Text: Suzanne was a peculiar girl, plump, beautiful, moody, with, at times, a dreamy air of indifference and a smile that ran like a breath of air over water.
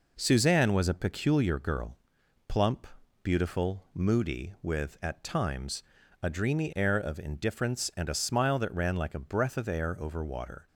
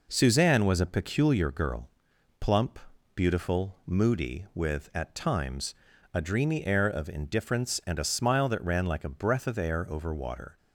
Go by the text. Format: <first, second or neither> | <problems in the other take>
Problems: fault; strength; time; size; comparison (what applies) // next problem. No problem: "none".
neither | none